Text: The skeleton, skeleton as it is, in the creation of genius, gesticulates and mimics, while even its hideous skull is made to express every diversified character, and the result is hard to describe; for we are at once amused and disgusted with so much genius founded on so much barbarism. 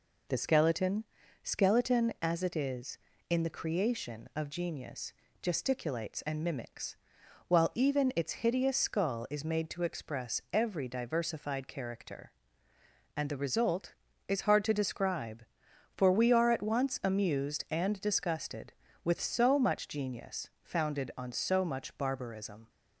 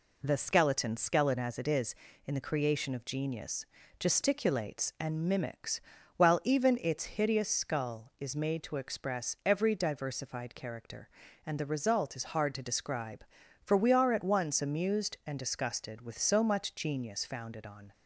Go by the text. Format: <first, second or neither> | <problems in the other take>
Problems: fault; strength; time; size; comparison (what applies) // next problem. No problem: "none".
first | stops before "so much barbarism"; at 17.9 s